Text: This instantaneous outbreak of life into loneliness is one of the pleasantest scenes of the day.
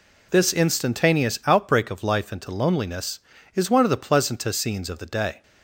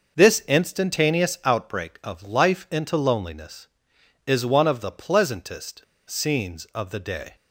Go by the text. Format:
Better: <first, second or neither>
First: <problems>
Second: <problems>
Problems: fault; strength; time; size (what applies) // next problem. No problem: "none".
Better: first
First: none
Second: pauses between "pleasantest" and "scenes"; slight; at 5.8 s; 0.24 s long